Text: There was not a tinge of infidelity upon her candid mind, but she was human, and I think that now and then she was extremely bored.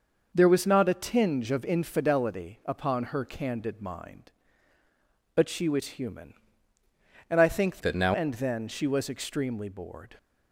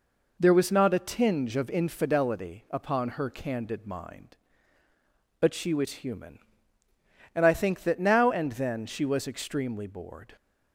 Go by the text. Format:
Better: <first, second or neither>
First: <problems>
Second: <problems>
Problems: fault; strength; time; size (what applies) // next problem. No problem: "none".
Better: second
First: changes voice from "that" to "now"; from 7.8 to 8.1 s; 0.3 s long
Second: none